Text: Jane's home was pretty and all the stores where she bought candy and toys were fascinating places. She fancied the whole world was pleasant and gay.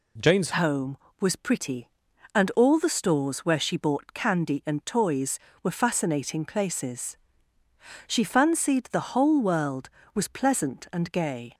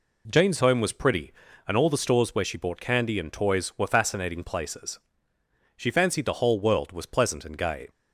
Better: second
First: changes voice at "home"; from 0.5 s on; 11.0 s long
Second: none

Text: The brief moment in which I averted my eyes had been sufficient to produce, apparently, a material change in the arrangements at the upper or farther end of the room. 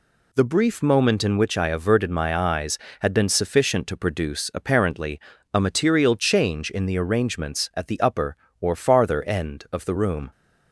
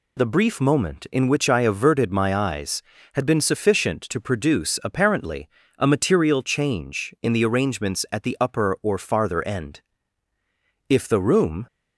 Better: first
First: none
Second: says "if" for "of"; at 10.8 s

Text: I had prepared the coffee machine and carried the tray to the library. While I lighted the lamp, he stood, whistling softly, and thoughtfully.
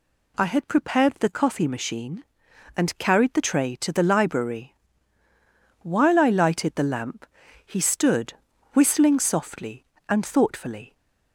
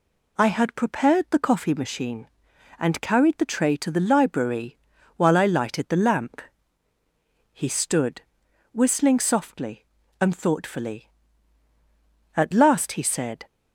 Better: first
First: none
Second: goes on to say "At last he said"; noticeable; from 12.3 s on; 1.1 s long

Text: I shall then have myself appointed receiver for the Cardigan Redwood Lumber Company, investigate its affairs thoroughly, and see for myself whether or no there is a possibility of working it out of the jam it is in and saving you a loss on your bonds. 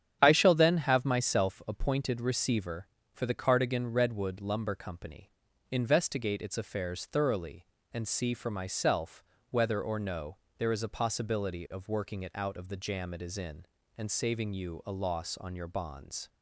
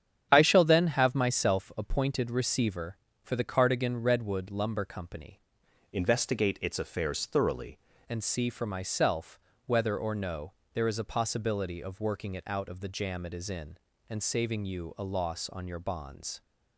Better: first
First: starts louder than the rest; strong; until 1.2 s; 9.5 dB // pauses between "myself" and "whether"; slight; at 9.2 s; 0.26 s long // pauses between "no" and "there"; slight; at 10.3 s; 0.22 s long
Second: starts louder than the rest; strong; until 1.3 s; 9 dB // changes voice from "investigate" to "thoroughly"; from 5.9 to 7.7 s; 1.8 s long // pauses between "myself" and "whether"; slight; at 9.3 s; 0.26 s long // pauses between "no" and "there"; slight; at 10.5 s; 0.22 s long

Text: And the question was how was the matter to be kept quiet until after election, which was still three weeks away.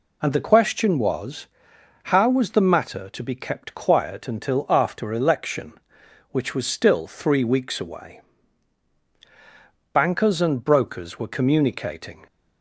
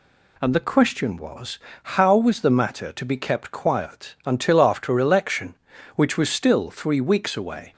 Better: second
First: pauses between "was" and "how"; noticeable; at 1.4 s; 0.58 s long // goes on to say "Bankers and brokers were communicating"; strong; from 9.9 s on; 2.3 s long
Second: pauses between "was" and "how"; slight; at 1.5 s; 0.24 s long

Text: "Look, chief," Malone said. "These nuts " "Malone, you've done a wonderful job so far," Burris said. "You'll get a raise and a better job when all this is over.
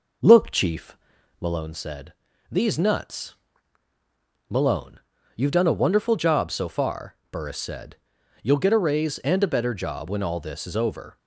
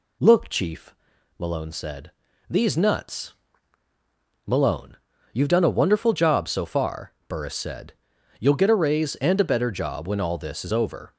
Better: second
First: starts louder than the rest; noticeable; until 1.7 s; 5 dB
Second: none

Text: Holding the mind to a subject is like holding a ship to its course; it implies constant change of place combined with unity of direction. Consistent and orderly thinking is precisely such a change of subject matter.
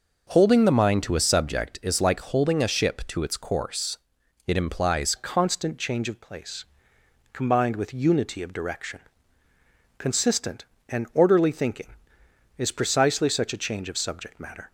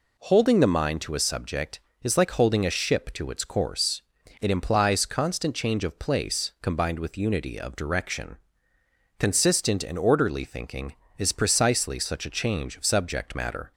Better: second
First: changes voice at "constant"; from 5.1 s on; 9.6 s long // pauses between "place" and "combined"; noticeable; at 6.6 s; 0.66 s long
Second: none

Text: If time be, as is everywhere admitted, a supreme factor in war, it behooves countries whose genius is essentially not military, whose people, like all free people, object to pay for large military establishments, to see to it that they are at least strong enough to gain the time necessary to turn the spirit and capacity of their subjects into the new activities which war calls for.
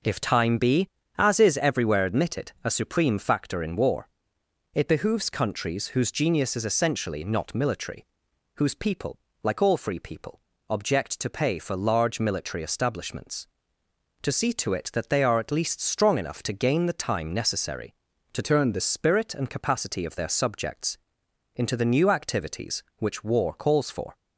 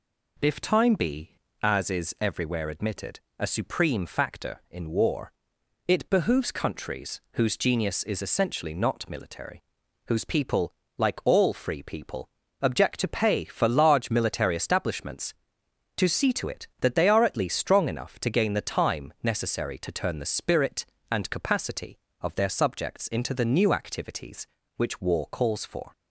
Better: second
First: changes voice from "turn" to "the"; from 18.4 to 18.8 s; 0.4 s long // pauses between "subjects" and "into"; noticeable; at 20.9 s; 0.58 s long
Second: none

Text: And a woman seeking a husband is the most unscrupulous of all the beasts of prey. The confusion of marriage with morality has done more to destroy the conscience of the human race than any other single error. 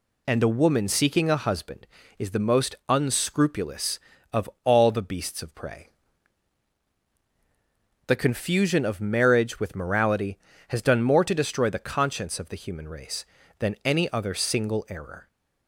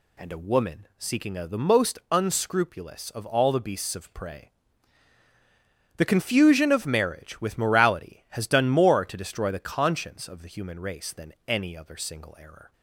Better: first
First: none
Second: skips "husband is"; at 1.4 s

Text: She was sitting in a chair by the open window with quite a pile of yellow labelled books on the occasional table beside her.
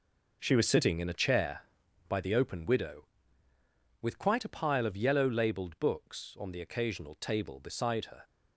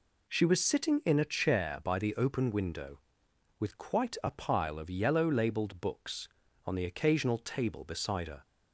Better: second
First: says "widow" for "window"; at 2.6 s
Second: none

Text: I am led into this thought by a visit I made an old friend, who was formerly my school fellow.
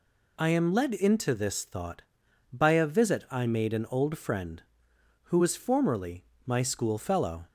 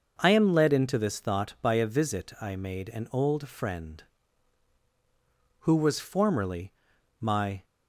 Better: first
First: pauses between "formerly" and "my"; slight; at 6.2 s; 0.24 s long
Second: pauses between "formerly" and "my"; noticeable; at 6.7 s; 0.48 s long // stops before "school fellow"; at 7.6 s

